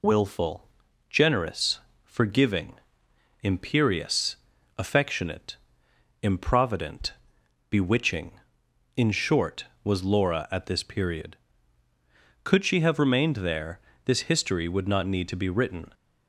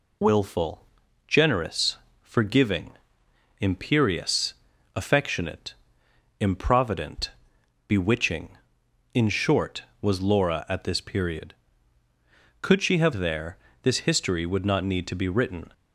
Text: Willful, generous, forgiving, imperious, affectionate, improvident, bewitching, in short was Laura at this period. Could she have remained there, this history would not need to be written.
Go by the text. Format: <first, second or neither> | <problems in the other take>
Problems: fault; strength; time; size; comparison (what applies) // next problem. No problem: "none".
first | skips "remained"; at 13.1 s